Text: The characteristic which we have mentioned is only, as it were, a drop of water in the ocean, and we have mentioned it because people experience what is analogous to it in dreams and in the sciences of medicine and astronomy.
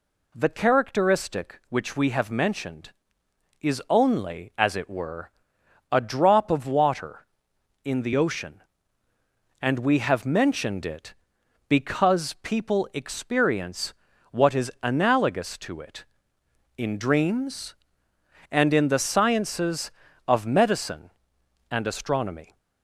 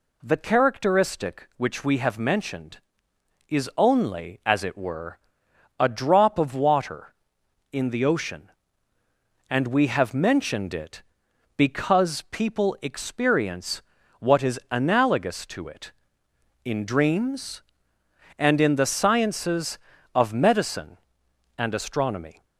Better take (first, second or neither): neither